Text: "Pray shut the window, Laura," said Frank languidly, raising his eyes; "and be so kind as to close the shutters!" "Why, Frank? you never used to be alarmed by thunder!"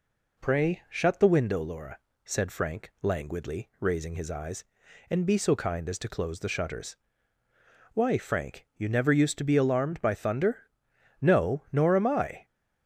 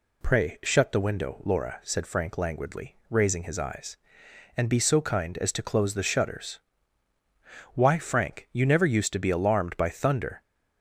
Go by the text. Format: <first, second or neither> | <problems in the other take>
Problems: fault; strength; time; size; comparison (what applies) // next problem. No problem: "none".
second | goes on to say "No nor am I"; noticeable; from 11.1 s on; 1.2 s long